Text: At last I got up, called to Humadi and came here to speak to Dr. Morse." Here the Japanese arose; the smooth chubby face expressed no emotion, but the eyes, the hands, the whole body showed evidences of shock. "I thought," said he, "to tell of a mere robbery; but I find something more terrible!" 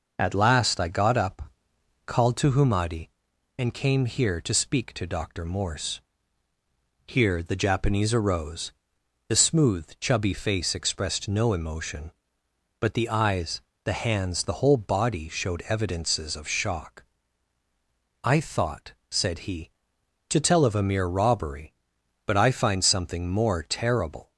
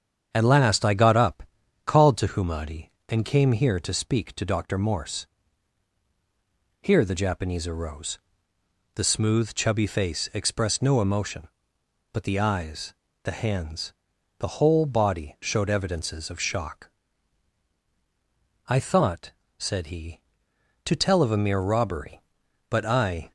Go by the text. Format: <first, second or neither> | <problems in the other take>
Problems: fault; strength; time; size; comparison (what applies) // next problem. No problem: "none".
first | starts louder than the rest; strong; until 1.3 s; 8 dB // stops before "find something more terrible"; at 23.2 s